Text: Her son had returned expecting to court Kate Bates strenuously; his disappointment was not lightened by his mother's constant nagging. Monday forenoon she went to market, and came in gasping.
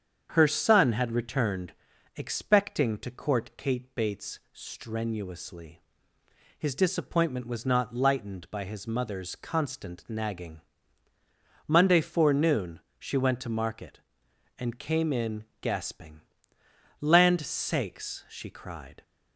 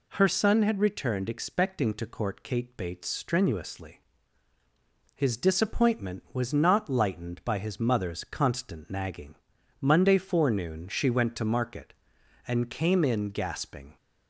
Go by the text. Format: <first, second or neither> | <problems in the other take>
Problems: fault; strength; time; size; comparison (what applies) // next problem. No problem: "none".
second | starts louder than the rest; strong; until 1.3 s; 8 dB // pauses between "returned" and "expecting"; at 1.7 s; 0.44 s long // pauses between "forenoon" and "she"; slight; at 12.7 s; 0.18 s long // pauses between "in" and "gasping"; slight; at 15.4 s; 0.18 s long // goes on to say "Land sakes she cried"; strong; from 17.0 s on; 2.0 s long